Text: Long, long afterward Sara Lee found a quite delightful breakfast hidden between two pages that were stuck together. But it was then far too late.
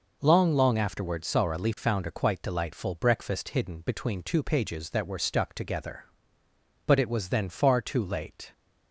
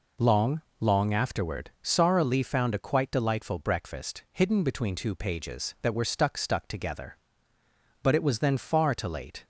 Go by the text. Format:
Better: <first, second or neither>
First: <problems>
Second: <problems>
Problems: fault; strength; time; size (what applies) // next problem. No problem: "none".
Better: first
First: none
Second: says "stuck" twice; at 6.3 s